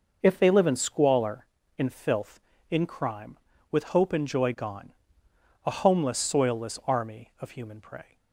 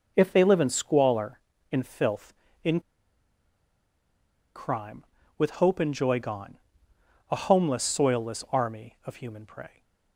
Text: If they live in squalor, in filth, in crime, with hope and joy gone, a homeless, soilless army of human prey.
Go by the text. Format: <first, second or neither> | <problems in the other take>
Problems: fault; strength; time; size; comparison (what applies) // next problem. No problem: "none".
first | pauses between "in" and "crime"; strong; at 2.7 s; 1.7 s long